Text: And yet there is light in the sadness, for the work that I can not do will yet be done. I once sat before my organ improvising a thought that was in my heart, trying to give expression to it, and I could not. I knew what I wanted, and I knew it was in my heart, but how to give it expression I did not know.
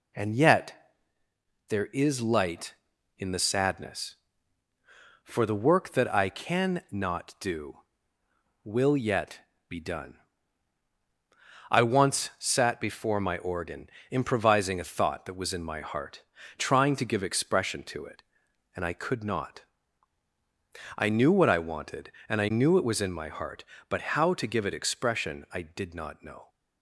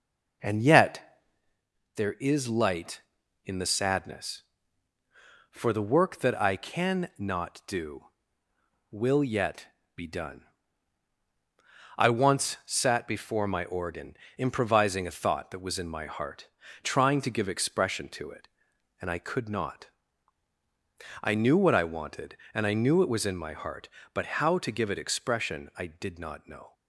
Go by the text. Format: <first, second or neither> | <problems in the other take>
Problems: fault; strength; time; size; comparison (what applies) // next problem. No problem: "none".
first | starts louder than the rest; noticeable; until 1.7 s; 5 dB // pauses between "yet" and "there"; noticeable; at 1.2 s; 0.74 s long; noticeable in the first // pauses between "yet" and "be"; slight; at 9.6 s; 0.28 s long; slight in the first // pauses between "organ" and "improvising"; slight; at 14.1 s; 0.22 s long; slight in the first